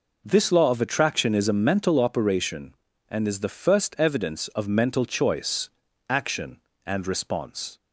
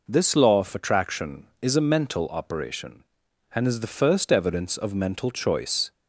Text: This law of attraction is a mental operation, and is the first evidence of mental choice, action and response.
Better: first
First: none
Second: stops before "action and response"; at 5.9 s

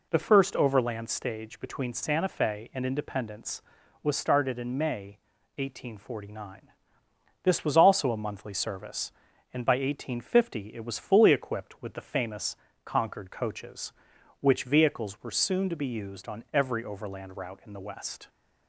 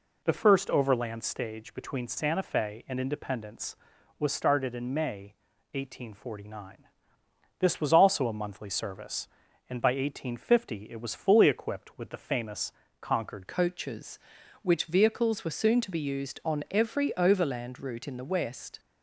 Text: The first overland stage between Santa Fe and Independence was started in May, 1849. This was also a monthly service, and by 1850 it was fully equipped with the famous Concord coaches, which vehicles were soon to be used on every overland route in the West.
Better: first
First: pauses between "famous" and "Concord"; slight; at 12.5 s; 0.30 s long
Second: pauses between "famous" and "Concord"; slight; at 12.7 s; 0.30 s long // changes voice at "coaches"; from 13.4 s on; 5.3 s long

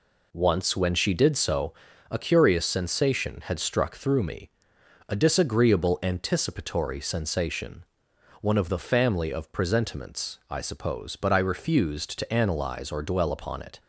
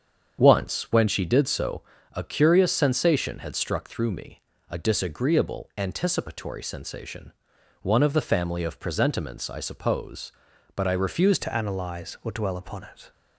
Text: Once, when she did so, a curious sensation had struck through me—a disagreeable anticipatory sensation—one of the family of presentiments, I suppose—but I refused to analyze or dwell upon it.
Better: first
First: none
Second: starts louder than the rest; strong; until 1.4 s; 7.5 dB // changes voice at "to"; from 11.4 s on; 1.7 s long

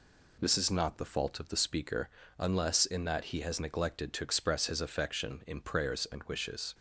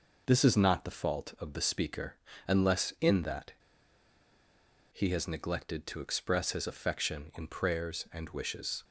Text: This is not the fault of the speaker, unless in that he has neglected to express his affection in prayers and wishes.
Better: first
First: none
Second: pauses between "that" and "he"; strong; at 3.5 s; 1.3 s long

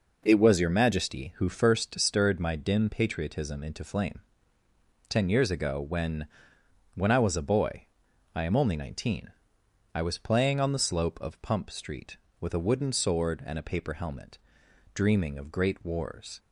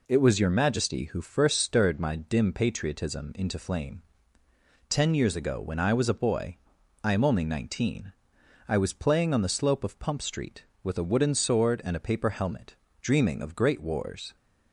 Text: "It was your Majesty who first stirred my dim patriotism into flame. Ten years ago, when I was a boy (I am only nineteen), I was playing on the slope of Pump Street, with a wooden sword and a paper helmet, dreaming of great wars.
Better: second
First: says "when" twice; at 6.9 s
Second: none

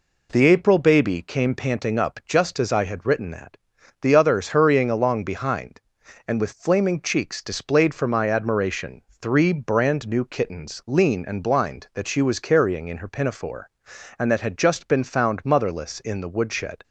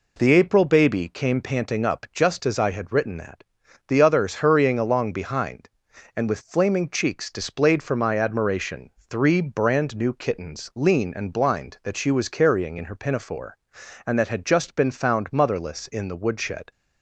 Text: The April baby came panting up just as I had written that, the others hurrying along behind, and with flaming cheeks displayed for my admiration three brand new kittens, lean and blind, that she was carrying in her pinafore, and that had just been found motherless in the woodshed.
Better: neither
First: pauses between "admiration" and "three"; slight; at 9.0 s; 0.22 s long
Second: pauses between "admiration" and "three"; slight; at 8.8 s; 0.22 s long

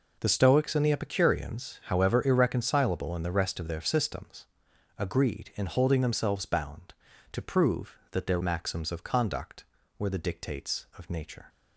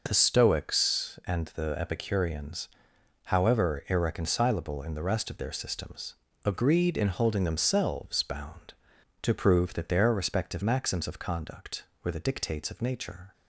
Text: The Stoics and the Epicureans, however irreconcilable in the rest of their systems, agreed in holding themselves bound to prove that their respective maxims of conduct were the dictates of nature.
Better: second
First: skips "respective"; at 8.4 s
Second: none

